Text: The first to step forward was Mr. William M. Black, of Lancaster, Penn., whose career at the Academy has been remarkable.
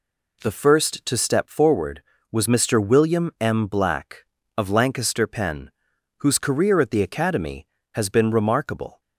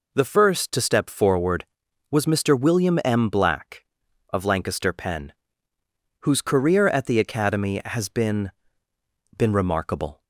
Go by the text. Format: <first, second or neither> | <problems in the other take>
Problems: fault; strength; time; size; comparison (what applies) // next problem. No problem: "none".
first | says "been" twice; at 9.3 s